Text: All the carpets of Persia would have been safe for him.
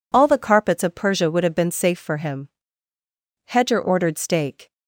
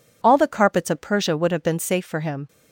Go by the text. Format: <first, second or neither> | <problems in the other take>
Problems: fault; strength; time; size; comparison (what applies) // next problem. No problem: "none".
second | goes on to say "Hedger ordered steak"; noticeable; from 3.4 s on; 1.2 s long